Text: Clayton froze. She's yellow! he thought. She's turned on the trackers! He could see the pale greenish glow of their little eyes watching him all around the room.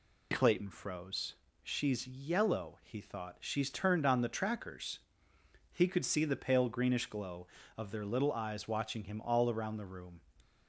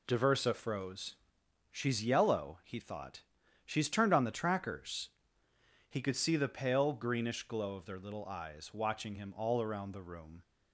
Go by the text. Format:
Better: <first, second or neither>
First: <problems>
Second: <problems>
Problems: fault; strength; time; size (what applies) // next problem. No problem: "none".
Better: first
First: none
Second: says "Diversa" for "Clayton"; at 0.0 s